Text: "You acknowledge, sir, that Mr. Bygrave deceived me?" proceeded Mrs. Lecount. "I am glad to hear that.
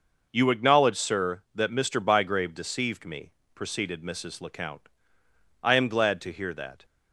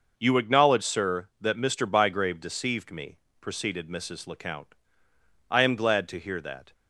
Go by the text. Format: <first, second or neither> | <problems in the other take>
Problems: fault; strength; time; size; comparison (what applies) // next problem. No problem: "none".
neither | none